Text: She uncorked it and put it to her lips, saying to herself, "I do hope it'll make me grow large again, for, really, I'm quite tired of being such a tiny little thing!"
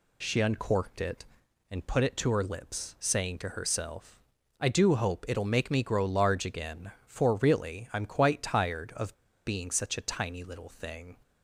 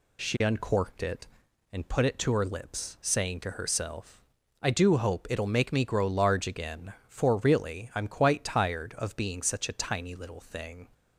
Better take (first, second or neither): second